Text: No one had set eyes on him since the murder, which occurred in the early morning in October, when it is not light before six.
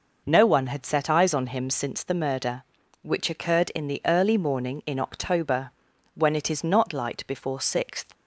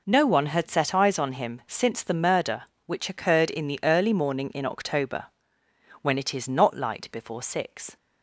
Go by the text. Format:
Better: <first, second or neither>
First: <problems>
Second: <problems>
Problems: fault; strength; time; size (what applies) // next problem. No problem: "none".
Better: second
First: says "sixth" for "six"; at 7.5 s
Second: none